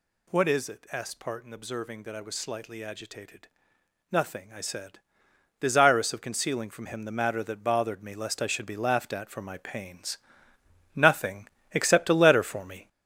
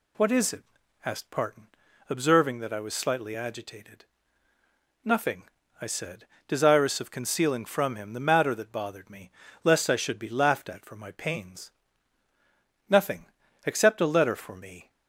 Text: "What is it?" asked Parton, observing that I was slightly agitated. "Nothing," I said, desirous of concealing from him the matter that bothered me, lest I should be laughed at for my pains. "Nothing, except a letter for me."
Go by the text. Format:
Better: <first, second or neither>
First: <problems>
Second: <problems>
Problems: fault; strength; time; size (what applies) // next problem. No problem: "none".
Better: second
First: gets louder; throughout; 6.5 dB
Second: none